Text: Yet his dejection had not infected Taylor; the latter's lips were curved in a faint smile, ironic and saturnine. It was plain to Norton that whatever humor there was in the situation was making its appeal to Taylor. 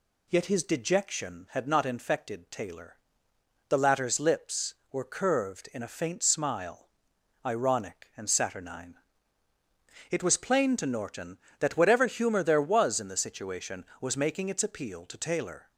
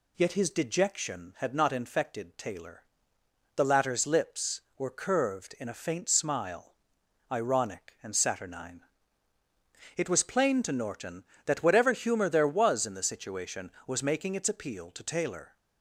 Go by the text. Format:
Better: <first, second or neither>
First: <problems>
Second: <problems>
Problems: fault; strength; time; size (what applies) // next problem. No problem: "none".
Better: neither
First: none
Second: none